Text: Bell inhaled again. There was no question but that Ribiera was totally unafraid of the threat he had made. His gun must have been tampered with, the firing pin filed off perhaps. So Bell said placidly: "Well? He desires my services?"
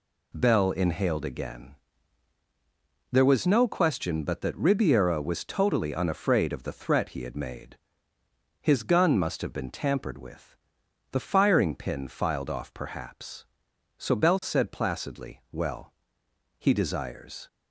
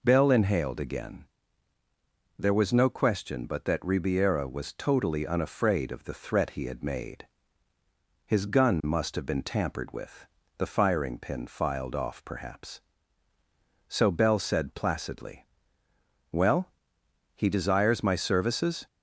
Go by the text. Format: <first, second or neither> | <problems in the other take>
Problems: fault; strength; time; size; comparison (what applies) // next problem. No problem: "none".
second | stops before "my services"; at 17.4 s